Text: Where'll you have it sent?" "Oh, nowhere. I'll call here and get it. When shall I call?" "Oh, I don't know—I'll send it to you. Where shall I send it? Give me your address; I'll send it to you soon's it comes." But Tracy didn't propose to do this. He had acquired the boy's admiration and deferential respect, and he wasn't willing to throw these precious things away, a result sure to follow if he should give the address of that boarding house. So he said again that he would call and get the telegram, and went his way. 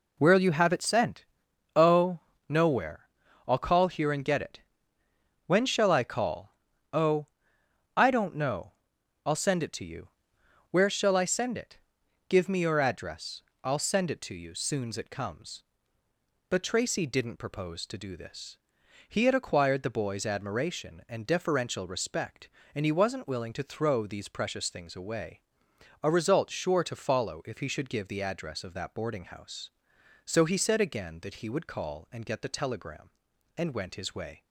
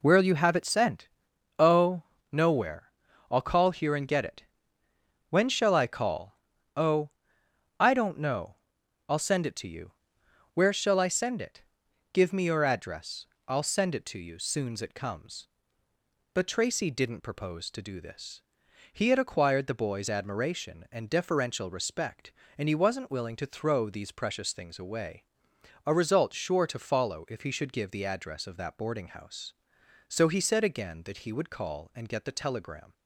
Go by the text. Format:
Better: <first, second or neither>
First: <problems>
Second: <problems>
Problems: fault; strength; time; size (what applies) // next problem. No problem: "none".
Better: first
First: none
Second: stops before "and went his way"; at 32.9 s